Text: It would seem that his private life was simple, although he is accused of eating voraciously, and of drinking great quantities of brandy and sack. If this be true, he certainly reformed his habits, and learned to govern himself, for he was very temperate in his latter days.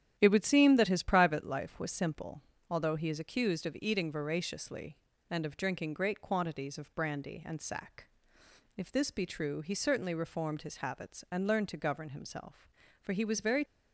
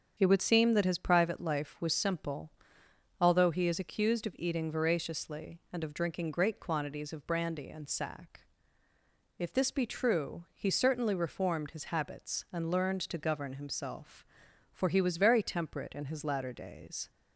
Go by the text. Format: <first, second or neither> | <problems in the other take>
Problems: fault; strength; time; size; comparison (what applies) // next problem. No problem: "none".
second | starts louder than the rest; strong; until 1.1 s; 10 dB; strong in the second // stops before "temperate in his latter days"; at 13.6 s